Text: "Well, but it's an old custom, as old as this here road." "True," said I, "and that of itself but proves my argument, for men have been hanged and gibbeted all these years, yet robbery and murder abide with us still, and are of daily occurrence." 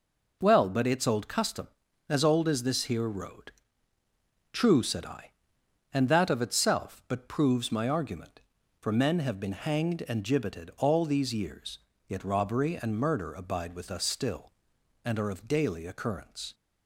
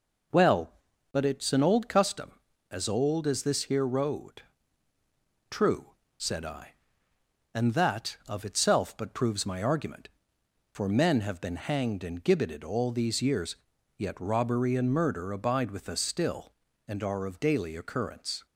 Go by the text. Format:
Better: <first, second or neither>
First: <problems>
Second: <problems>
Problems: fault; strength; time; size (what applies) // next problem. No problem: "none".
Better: second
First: skips "an"; at 1.0 s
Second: none